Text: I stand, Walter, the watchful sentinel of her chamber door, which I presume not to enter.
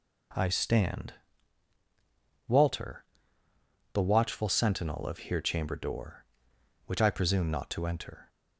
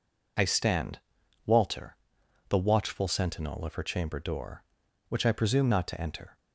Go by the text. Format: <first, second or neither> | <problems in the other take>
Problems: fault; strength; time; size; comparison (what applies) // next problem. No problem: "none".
second | says "here" for "her"; at 5.1 s